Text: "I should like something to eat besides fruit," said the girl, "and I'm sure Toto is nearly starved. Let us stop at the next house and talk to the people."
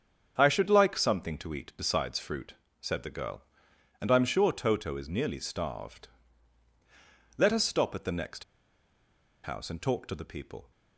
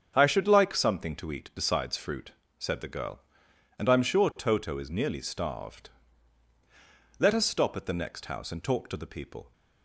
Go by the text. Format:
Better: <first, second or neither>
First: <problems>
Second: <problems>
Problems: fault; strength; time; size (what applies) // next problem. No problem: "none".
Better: second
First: starts louder than the rest; strong; until 1.3 s; 7.5 dB // pauses between "next" and "house"; at 8.4 s; 1.0 s long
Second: starts louder than the rest; strong; until 1.1 s; 7.5 dB